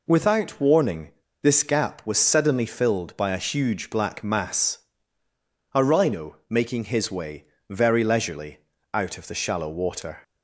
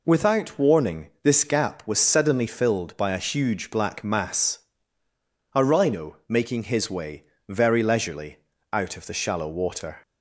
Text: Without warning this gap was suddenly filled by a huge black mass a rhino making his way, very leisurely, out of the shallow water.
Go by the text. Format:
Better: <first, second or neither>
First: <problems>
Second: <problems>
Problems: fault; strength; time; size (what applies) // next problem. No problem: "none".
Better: second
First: pauses between "warning" and "this"; slight; at 1.1 s; 0.31 s long // pauses between "mass" and "a"; noticeable; at 4.7 s; 0.98 s long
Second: pauses between "mass" and "a"; noticeable; at 4.5 s; 0.98 s long